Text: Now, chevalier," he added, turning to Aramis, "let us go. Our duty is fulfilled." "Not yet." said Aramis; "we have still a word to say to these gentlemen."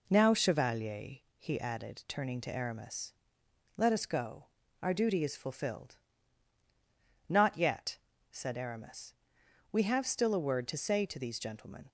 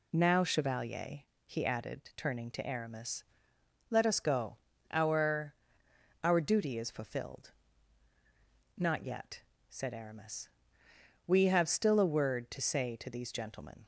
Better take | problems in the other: first | says "Our" twice; at 6.2 s

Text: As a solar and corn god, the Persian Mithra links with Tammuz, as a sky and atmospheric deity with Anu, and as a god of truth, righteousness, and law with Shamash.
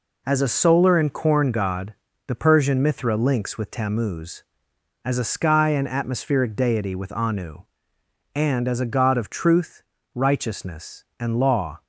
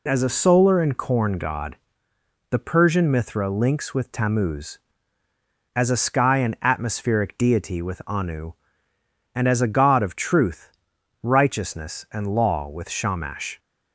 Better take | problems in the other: second | stops before "with Shamash"; at 11.8 s

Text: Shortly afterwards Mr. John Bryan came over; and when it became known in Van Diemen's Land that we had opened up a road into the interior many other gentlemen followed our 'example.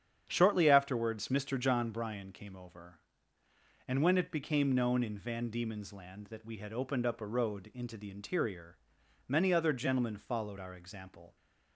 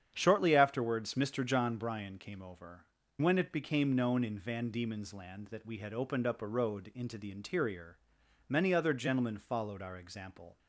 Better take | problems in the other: first | starts louder than the rest; strong; until 1.1 s; 8.5 dB; strong in the first // skips "and"; at 3.0 s // pauses between "interior" and "many"; noticeable; at 7.9 s; 0.50 s long; noticeable in the first

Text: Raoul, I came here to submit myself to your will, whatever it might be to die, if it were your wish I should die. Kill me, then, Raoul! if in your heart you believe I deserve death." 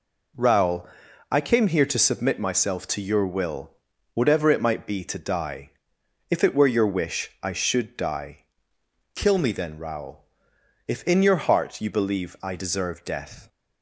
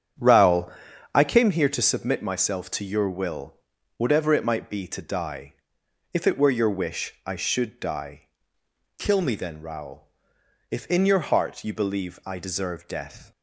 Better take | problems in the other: first | starts louder than the rest; strong; until 1.6 s; 8.5 dB

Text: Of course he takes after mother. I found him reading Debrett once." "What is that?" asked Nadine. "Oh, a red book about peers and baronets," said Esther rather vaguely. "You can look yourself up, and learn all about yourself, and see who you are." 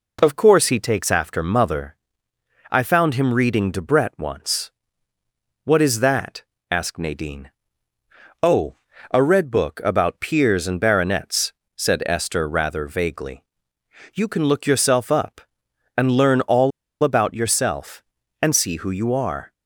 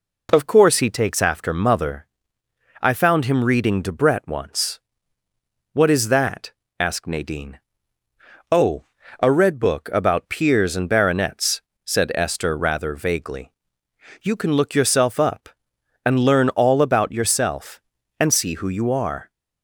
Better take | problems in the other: second | pauses between "all" and "about"; slight; at 16.7 s; 0.33 s long

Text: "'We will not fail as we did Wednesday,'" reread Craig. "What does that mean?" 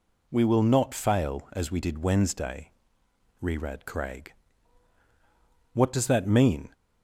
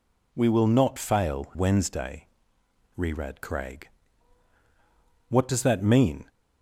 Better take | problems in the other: first | skips "as we did"; at 1.5 s

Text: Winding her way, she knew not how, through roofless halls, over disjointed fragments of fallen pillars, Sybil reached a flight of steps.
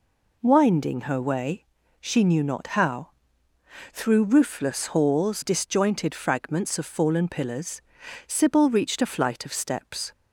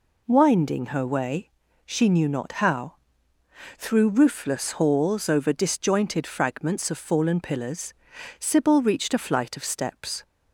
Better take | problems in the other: second | skips "over"; at 5.4 s

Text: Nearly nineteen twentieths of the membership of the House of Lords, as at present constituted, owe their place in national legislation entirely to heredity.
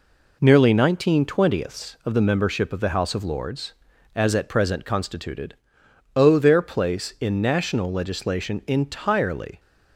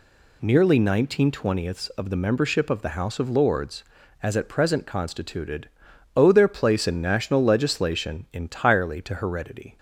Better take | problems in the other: second | stops before "to heredity"; at 9.5 s

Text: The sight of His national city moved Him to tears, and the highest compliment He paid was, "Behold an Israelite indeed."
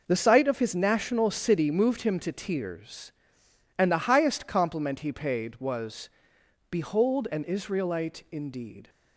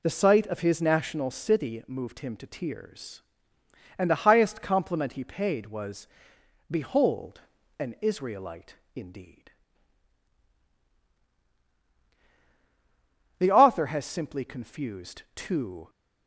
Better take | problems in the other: first | pauses between "Behold" and "an"; at 7.3 s; 0.40 s long // pauses between "Israelite" and "indeed"; slight; at 8.7 s; 0.18 s long // goes on to say "The author has simply confused two"; strong; from 13.3 s on; 2.5 s long

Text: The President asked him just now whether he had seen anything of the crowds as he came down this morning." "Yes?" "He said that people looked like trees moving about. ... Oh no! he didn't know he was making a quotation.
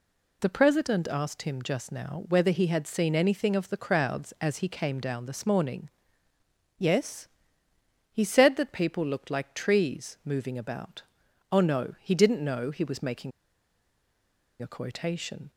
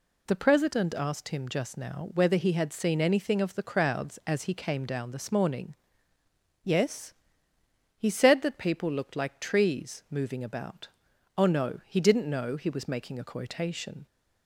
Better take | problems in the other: second | pauses between "making" and "a"; strong; at 13.3 s; 1.3 s long

